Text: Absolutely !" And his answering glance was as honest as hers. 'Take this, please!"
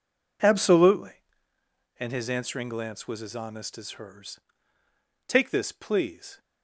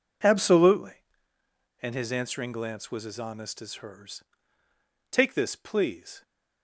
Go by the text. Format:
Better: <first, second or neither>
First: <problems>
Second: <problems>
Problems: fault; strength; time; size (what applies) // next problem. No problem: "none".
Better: neither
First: none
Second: none